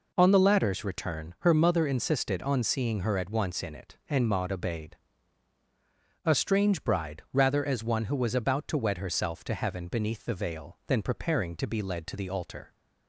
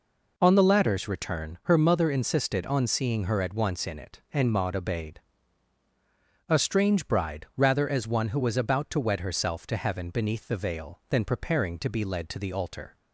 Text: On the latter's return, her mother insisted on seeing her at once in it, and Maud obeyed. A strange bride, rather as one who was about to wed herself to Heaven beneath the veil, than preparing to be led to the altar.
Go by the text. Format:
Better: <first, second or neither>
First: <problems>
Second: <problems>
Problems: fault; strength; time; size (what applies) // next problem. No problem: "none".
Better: neither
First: none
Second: none